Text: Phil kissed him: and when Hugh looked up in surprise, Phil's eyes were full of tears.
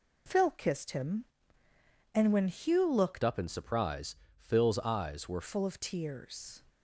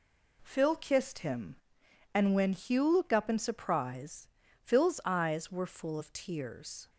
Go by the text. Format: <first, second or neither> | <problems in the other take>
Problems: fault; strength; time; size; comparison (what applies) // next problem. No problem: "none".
second | changes voice from "up" to "were"; from 3.2 to 5.4 s; 2.2 s long